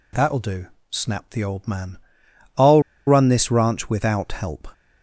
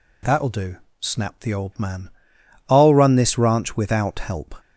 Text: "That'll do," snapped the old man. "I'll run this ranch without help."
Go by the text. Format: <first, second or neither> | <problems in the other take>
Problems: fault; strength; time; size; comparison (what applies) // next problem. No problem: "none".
second | pauses between "I'll" and "run"; slight; at 2.8 s; 0.26 s long